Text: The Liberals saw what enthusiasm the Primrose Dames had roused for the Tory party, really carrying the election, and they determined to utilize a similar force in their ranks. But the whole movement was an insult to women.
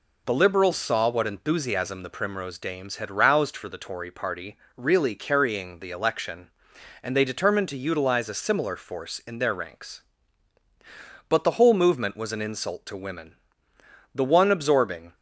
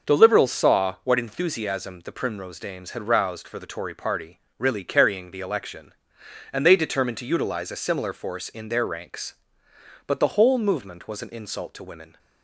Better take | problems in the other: second | goes on to say "The one absorbing"; noticeable; from 14.1 s on; 1.0 s long

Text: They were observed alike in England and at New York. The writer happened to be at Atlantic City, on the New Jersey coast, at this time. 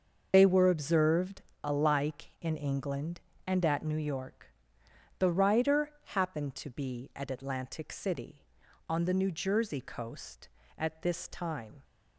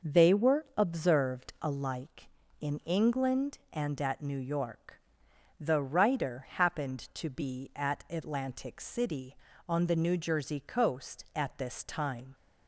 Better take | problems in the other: second | loses the start of "They"; at 0.3 s; 45 ms // starts louder than the rest; until 1.3 s; 6.5 dB; noticeable in the second // pauses between "observed" and "alike"; slight; at 1.4 s; 0.22 s long

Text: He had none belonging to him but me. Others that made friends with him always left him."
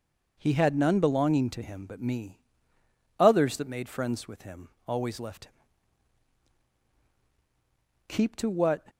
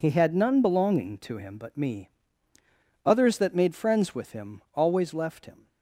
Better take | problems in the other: second | pauses between "him" and "always"; slight; at 4.6 s; 0.18 s long // goes on to say "Keep to what"; noticeable; from 8.0 s on; 0.80 s long

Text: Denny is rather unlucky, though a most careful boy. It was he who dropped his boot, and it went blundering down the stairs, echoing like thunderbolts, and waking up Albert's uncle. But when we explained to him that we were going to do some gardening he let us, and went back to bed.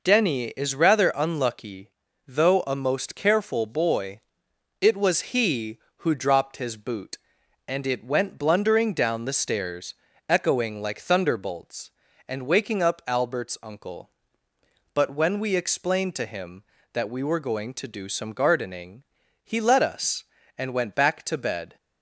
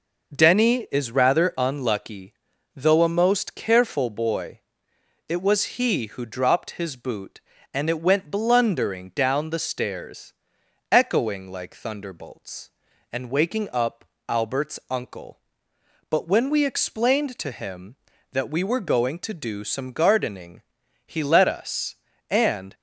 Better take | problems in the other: first | pauses between "up" and "Albert's"; slight; at 14.0 s; 0.20 s long // pauses between "gardening" and "he"; noticeable; at 20.6 s; 0.48 s long; also in the first // stops before "went back to bed"; at 22.7 s

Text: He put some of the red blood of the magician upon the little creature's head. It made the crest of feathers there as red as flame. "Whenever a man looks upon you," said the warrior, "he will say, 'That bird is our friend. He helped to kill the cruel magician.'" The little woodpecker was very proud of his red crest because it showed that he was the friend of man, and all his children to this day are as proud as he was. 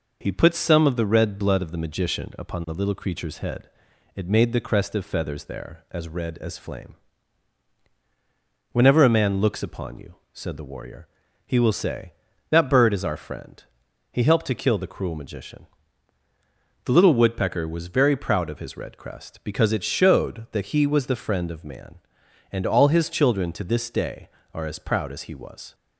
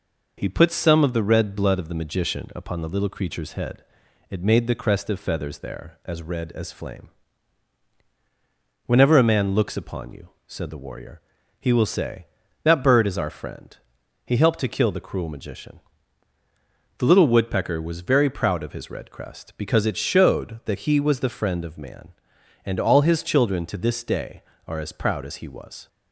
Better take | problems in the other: neither | none

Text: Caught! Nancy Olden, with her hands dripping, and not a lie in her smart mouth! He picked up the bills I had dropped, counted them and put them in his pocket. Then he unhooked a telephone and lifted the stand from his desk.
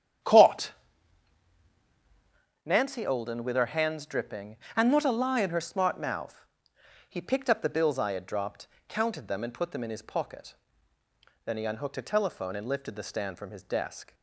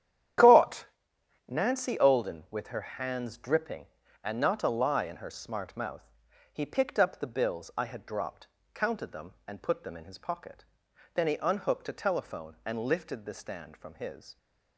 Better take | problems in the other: first | starts louder than the rest; strong; until 2.0 s; 10.5 dB; strong in the first // stops before "desk"; at 14.3 s

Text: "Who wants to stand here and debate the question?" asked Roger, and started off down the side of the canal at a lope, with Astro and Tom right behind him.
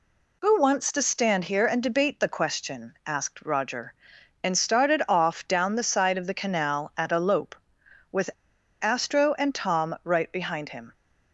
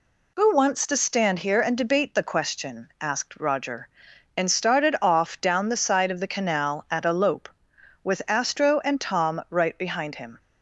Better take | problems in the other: second | pauses between "with" and "Astro"; noticeable; at 8.3 s; 0.51 s long

